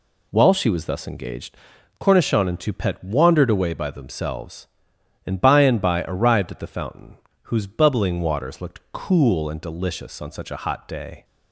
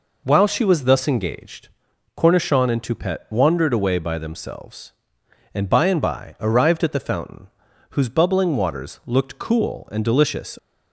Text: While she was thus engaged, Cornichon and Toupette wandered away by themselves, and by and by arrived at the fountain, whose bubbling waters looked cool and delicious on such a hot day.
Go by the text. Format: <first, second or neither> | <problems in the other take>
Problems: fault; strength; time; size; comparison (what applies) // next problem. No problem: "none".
first | stops before "on such a hot day"; at 10.5 s